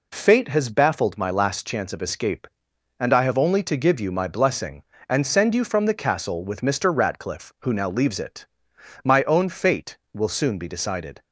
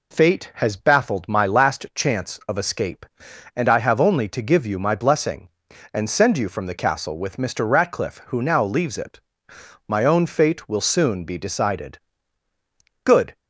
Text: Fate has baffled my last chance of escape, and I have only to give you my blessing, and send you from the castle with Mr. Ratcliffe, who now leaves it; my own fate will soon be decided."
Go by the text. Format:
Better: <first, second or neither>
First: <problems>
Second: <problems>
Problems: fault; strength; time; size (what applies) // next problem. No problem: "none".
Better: first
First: none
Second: goes on to say "Good"; slight; from 13.0 s on; 0.30 s long